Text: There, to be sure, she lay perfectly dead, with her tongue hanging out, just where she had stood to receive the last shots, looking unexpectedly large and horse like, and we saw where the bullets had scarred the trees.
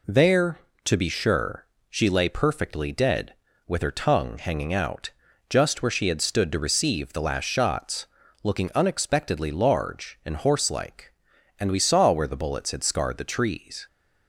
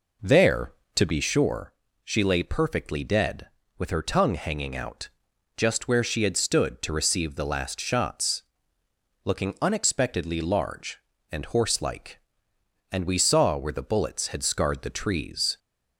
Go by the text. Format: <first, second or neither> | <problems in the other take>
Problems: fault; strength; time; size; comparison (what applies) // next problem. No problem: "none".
first | starts louder than the rest; noticeable; until 1.4 s; 4.5 dB